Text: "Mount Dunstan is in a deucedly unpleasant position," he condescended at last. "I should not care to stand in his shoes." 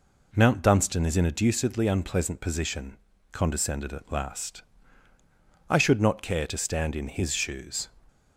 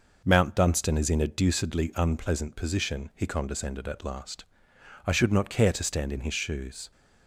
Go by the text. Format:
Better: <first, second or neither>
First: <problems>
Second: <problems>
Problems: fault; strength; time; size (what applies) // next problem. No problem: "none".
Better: second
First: skips "he"; at 3.1 s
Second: none